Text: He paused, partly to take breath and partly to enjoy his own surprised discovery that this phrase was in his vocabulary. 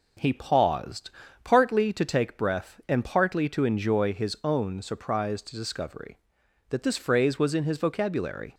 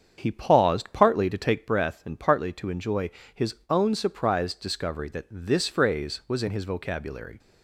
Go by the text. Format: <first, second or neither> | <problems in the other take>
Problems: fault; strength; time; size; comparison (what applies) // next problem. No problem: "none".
first | starts louder than the rest; strong; until 1.6 s; 7.5 dB // pauses between "enjoy" and "his"; slight; at 3.0 s; 0.24 s long